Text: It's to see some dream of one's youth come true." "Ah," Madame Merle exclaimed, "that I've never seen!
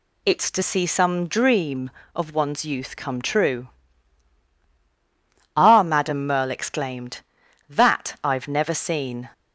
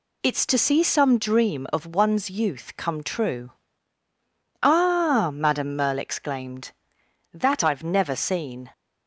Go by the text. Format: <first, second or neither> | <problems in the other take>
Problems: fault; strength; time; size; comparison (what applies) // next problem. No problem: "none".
neither | none